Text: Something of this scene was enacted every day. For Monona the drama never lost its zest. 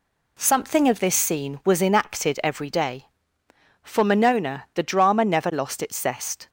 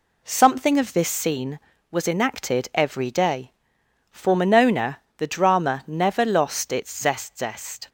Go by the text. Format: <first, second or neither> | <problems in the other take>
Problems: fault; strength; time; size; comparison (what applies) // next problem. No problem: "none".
first | pauses between "Monona" and "the"; slight; at 4.9 s; 0.18 s long // says "zest" twice; at 7.3 s